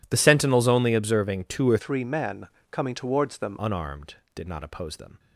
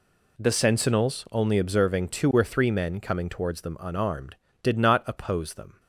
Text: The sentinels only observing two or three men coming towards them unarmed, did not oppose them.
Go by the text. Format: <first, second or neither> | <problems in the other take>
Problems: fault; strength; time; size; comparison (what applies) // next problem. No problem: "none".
second | changes voice from "three" to "them"; from 1.7 to 3.5 s; 1.8 s long // pauses between "men" and "coming"; slight; at 2.4 s; 0.22 s long